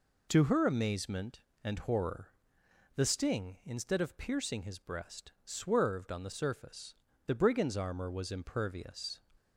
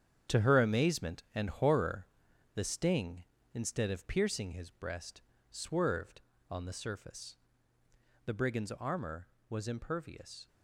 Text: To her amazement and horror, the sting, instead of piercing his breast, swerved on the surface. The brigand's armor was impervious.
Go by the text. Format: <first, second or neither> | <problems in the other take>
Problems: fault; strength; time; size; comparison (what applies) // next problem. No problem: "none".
first | gets quieter; strong; throughout; 9.5 dB